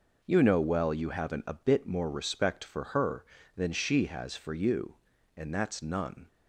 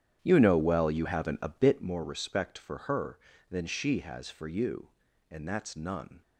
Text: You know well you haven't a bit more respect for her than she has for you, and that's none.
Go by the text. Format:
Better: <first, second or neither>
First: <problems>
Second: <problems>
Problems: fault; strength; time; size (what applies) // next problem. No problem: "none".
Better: first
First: none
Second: starts louder than the rest; strong; until 1.9 s; 10 dB